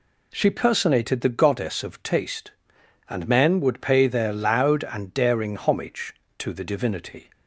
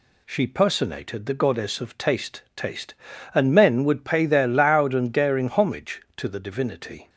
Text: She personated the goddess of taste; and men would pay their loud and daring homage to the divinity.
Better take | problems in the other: first | says "taste" twice; at 2.5 s

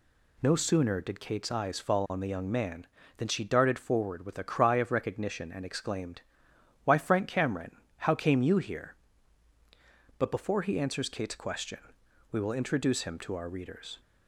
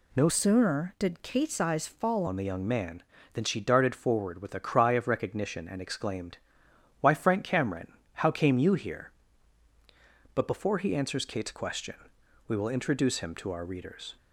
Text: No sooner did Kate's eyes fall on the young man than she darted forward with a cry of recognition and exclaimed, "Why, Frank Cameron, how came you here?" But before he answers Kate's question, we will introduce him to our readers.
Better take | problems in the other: first | changes voice from "sooner" to "fall"; from 0.2 to 2.2 s; 2.0 s long

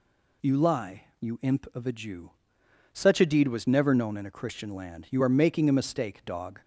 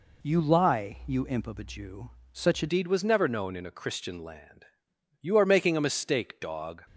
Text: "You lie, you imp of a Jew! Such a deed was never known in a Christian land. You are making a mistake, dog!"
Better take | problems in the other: first | changes voice at "deed"; from 2.6 s on; 4.2 s long

